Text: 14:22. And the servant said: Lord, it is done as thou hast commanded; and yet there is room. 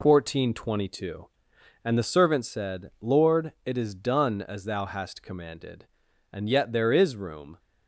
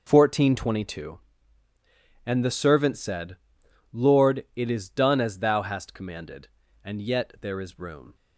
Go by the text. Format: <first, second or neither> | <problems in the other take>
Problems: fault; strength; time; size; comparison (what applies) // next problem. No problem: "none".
neither | none